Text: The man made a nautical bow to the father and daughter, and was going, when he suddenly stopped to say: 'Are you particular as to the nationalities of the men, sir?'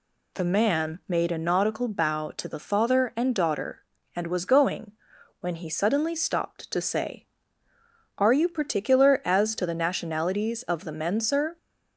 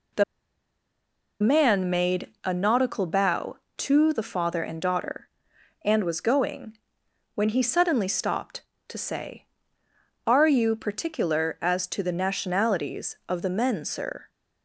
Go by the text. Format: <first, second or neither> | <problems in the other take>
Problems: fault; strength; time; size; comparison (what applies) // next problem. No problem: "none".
first | pauses between "The" and "man"; at 0.2 s; 1.1 s long